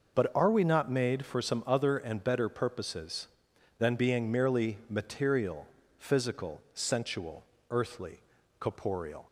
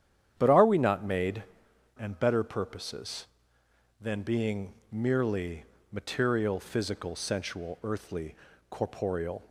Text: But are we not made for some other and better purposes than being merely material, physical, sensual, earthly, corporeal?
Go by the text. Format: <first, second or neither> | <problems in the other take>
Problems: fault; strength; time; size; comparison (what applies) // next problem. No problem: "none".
first | starts louder than the rest; strong; until 1.3 s; 9.5 dB // skips "for some other"; at 1.7 s // pauses between "being" and "merely"; slight; at 4.7 s; 0.18 s long // pauses between "merely" and "material"; slight; at 5.6 s; 0.28 s long